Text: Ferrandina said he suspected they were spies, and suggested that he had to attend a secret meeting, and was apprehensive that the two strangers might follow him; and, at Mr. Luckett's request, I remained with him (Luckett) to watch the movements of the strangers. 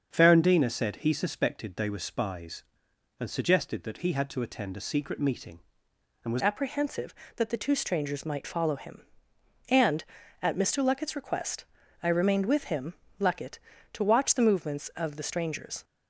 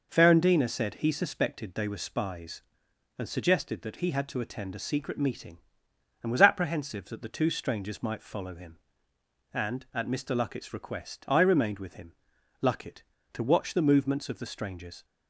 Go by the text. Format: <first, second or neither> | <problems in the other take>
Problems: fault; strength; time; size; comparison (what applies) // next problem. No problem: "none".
second | starts louder than the rest; until 1.1 s; 6.5 dB // changes voice at "apprehensive"; from 6.3 s on; 9.5 s long